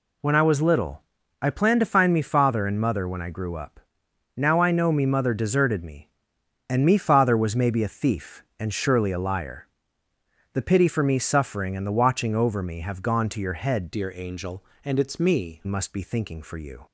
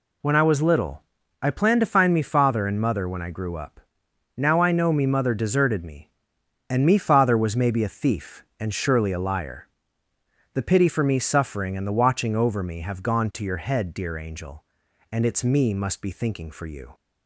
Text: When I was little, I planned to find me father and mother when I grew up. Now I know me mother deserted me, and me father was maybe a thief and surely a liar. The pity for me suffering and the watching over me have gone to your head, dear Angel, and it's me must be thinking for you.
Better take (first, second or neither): second